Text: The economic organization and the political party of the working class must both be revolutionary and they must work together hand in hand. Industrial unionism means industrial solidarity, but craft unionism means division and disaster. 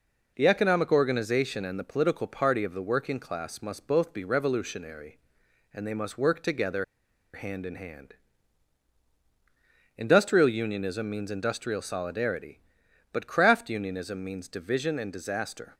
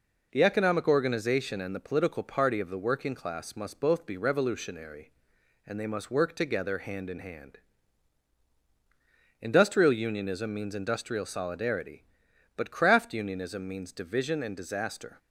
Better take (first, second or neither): second